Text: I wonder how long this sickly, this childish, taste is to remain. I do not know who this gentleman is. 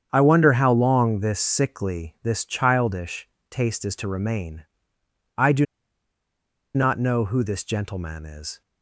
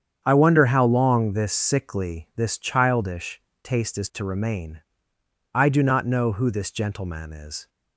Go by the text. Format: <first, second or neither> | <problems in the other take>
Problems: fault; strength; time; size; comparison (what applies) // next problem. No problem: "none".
second | starts louder than the rest; strong; until 1.1 s; 8 dB; strong in the second // pauses between "do" and "not"; at 5.6 s; 1.1 s long